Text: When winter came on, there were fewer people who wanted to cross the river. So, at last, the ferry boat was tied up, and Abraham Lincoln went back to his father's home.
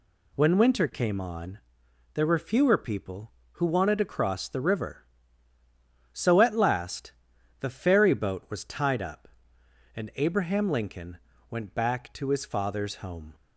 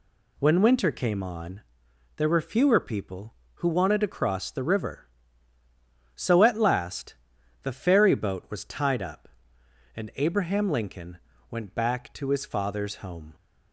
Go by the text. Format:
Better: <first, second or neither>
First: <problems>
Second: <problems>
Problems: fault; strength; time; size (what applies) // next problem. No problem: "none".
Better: neither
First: pauses between "Lincoln" and "went"; slight; at 11.1 s; 0.32 s long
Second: pauses between "Lincoln" and "went"; slight; at 11.1 s; 0.32 s long